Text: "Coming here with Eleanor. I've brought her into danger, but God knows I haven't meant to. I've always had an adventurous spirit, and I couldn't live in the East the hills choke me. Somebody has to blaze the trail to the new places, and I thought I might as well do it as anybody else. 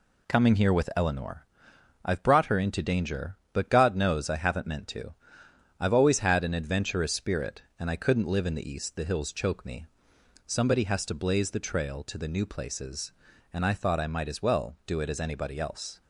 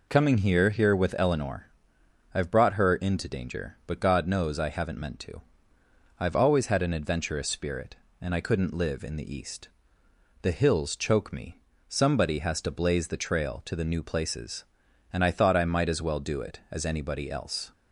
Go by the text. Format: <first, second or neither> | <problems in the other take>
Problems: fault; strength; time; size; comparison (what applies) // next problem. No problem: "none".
first | says "here" twice; at 0.6 s // pauses between "East" and "the"; noticeable; at 9.6 s; 0.74 s long